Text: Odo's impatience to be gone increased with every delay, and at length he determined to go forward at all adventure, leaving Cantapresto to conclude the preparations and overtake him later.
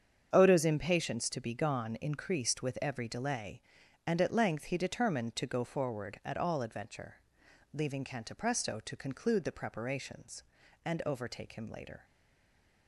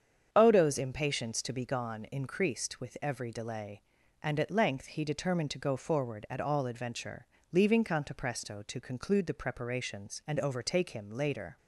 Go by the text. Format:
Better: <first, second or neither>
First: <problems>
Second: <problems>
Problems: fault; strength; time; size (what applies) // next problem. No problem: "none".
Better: second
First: starts louder than the rest; strong; until 1.3 s; 7.5 dB // stays silent after the last word; slight; from 12.0 s on; 0.8 s long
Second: starts louder than the rest; strong; until 1.3 s; 7.5 dB